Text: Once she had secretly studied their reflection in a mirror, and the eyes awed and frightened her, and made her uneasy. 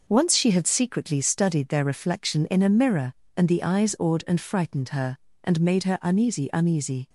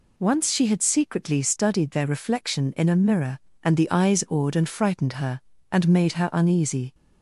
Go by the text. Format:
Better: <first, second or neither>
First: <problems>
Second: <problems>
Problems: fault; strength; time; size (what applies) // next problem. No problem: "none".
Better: second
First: says "uneasy" twice; at 6.5 s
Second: none